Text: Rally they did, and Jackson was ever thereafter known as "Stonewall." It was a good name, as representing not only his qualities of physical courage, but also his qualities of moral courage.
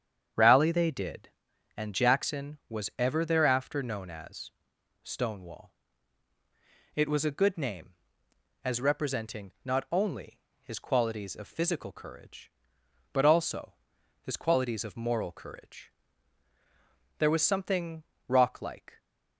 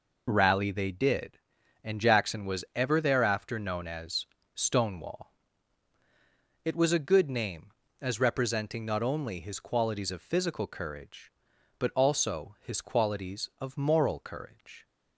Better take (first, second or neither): second